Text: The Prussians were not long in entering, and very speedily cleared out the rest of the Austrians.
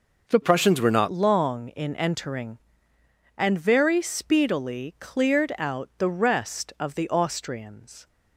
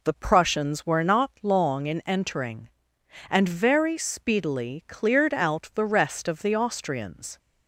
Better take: second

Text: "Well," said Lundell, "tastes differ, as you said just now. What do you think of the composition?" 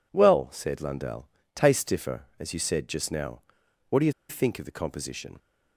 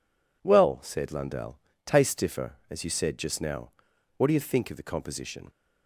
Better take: second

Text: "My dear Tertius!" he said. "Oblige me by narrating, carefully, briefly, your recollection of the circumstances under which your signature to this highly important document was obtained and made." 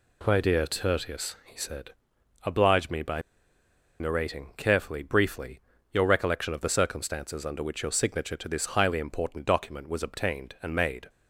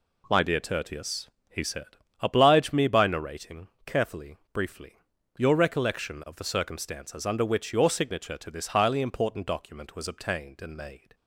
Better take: second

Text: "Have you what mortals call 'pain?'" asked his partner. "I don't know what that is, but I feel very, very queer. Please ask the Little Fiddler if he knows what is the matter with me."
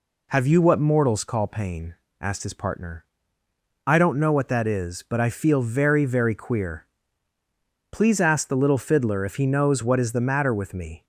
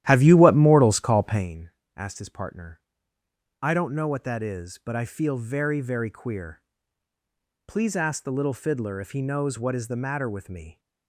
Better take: first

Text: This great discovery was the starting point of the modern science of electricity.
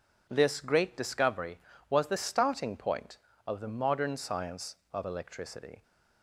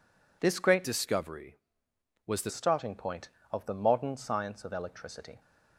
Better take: first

